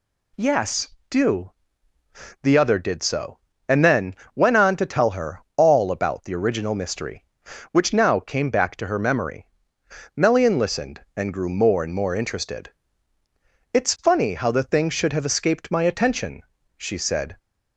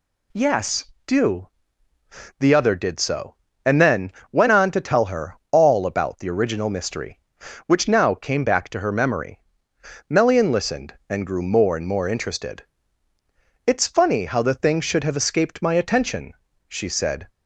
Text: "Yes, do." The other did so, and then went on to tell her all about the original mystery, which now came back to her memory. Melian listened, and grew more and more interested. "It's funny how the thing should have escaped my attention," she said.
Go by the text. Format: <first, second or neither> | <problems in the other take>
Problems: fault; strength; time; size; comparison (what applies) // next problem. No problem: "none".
neither | pauses between "then" and "went"; slight; the same in both